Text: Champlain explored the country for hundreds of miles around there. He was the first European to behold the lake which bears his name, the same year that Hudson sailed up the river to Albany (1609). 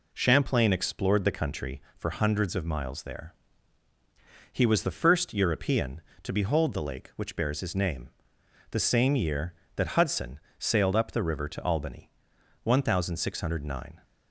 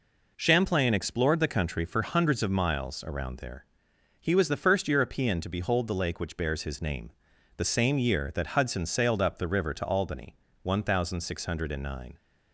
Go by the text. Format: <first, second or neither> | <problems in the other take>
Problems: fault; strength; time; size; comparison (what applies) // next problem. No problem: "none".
second | skips "around"; at 3.0 s // pauses between "Hudson" and "sailed"; slight; at 10.3 s; 0.20 s long